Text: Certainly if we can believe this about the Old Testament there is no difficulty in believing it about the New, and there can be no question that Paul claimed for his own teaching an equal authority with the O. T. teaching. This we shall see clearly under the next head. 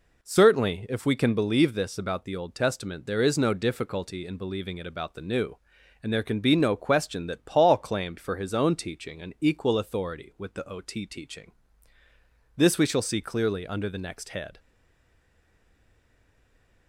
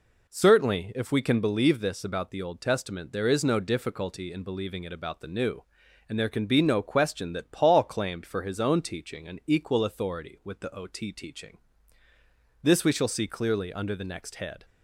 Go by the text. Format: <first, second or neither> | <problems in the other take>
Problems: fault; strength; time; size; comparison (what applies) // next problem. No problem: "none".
second | stays silent after the last word; from 14.5 s on; 2.3 s long